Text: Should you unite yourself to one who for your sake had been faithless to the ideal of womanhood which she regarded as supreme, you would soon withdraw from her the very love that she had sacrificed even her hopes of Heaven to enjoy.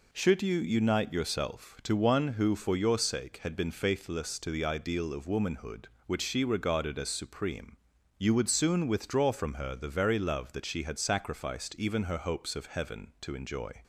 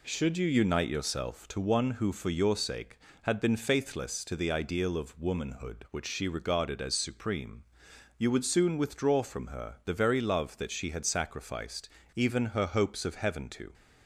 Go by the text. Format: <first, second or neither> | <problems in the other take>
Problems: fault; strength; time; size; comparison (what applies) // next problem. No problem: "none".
first | pauses between "sacrificed" and "even"; slight; at 11.8 s; 0.25 s long // stops before "enjoy"; at 13.7 s